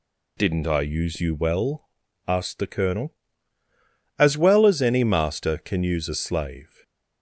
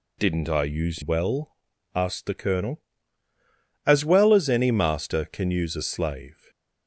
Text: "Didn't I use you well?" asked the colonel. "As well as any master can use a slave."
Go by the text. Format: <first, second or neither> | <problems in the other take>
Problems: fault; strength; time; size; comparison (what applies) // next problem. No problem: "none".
first | skips "you"; at 1.0 s